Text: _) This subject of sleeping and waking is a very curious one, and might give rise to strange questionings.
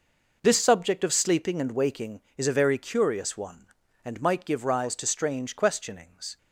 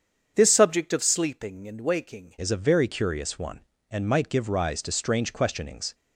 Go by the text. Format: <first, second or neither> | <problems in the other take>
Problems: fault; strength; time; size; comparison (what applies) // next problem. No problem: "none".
first | starts louder than the rest; strong; until 1.3 s; 7.5 dB // changes voice at "is"; from 2.3 s on; 3.6 s long